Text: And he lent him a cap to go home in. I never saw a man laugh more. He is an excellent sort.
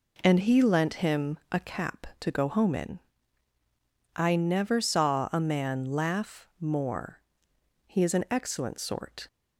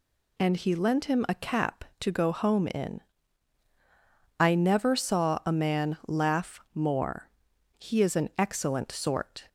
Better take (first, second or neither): neither